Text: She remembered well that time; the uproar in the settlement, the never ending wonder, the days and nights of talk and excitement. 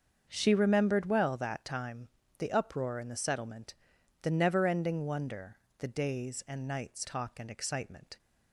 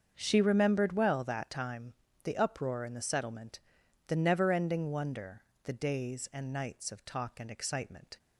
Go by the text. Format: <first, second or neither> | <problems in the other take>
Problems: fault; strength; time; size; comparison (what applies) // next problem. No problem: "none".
second | starts louder than the rest; until 1.3 s; 6.5 dB; also in the second // skips "of"; at 7.0 s